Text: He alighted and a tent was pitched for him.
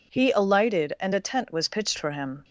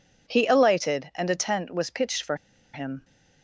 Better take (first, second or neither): first